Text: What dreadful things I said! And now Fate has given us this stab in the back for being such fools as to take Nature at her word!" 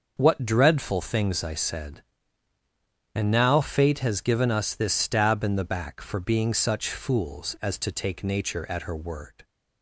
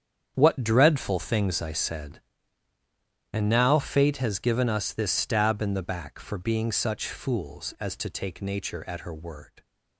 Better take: first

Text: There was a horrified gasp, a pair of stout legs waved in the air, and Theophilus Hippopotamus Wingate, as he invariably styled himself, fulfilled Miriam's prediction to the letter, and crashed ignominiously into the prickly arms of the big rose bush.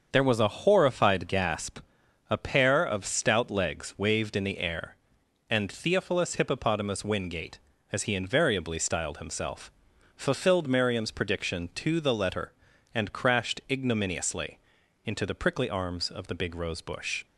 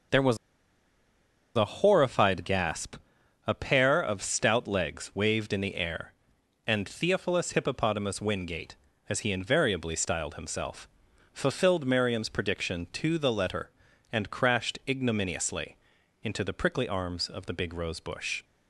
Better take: first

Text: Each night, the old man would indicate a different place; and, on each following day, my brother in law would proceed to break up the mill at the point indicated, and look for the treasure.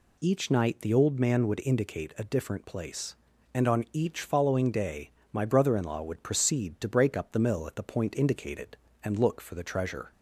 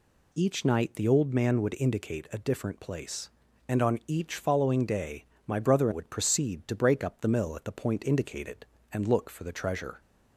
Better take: first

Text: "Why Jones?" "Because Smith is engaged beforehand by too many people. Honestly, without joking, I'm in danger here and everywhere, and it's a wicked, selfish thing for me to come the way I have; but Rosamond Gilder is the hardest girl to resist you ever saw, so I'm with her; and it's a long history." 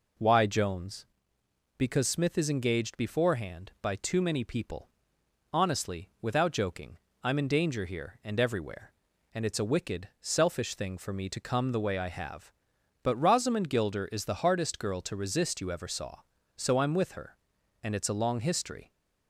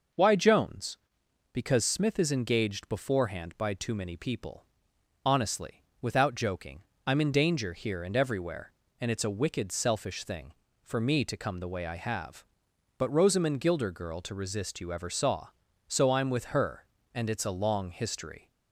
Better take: first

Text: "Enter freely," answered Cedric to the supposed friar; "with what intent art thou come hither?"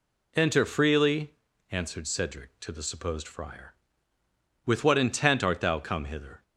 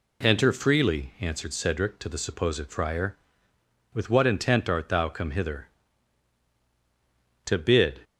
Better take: first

